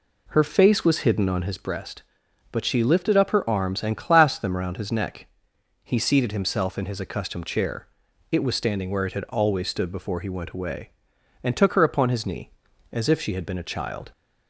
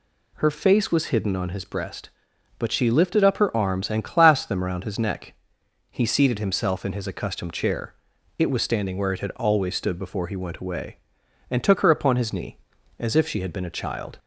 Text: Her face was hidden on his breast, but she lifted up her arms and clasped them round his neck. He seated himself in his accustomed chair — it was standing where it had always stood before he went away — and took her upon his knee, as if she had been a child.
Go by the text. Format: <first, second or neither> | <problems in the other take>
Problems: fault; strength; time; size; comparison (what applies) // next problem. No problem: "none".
second | starts louder than the rest; slight; until 1.7 s; 2.5 dB